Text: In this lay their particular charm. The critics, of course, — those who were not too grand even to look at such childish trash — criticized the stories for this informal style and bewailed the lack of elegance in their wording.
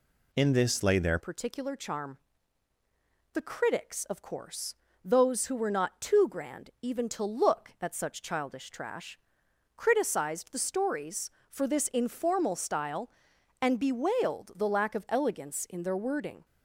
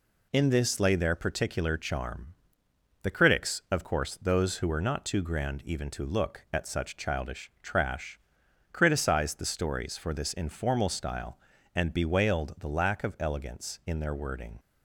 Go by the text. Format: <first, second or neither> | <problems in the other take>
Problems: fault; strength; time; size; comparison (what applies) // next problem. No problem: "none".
second | changes voice at "particular"; from 1.1 s on; 15.3 s long